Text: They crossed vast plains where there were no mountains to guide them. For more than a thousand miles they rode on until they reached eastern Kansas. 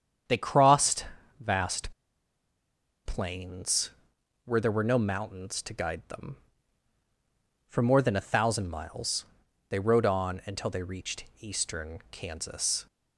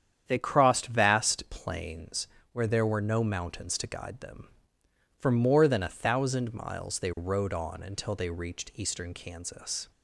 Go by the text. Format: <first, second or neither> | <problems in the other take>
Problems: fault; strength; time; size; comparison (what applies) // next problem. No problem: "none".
second | starts louder than the rest; strong; until 1.6 s; 8 dB; strong in the second // pauses between "crossed" and "vast"; slight; at 1.0 s; 0.34 s long // pauses between "vast" and "plains"; at 1.9 s; 1.1 s long // pauses between "plains" and "where"; noticeable; at 3.9 s; 0.54 s long; slight in the second // pauses between "miles" and "they"; at 9.2 s; 0.44 s long // pauses between "reached" and "eastern"; slight; at 11.2 s; 0.16 s long